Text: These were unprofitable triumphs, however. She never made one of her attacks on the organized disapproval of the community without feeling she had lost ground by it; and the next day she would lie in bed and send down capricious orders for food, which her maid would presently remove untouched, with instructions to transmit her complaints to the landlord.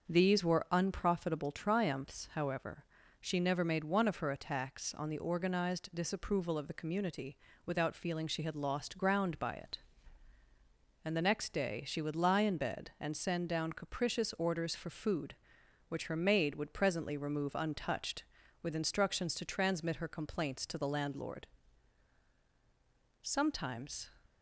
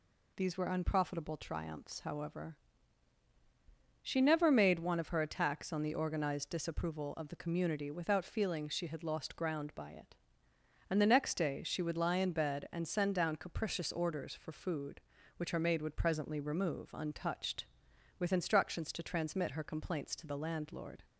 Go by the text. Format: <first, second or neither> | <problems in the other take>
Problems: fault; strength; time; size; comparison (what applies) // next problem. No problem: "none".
second | starts louder than the rest; until 1.1 s; 6.5 dB // pauses between "community" and "without"; slight; at 7.3 s; 0.28 s long // goes on to say "Sometimes"; noticeable; from 23.2 s on; 0.88 s long